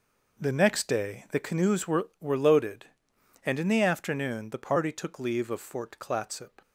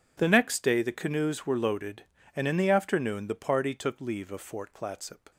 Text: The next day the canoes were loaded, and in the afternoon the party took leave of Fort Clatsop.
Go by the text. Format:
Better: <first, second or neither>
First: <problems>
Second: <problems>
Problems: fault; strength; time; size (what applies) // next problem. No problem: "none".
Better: second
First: says "were" twice; at 2.2 s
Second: none